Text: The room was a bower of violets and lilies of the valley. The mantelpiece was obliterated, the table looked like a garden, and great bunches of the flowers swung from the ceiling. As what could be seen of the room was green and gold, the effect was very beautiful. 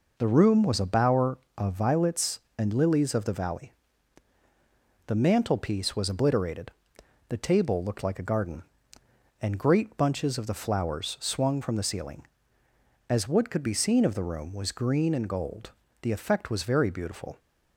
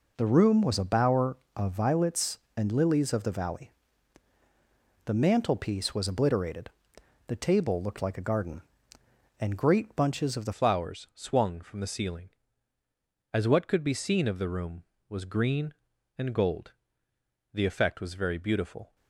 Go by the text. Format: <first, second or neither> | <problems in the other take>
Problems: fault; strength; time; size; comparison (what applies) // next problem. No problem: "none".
first | changes voice at "flowers"; from 10.5 s on; 8.4 s long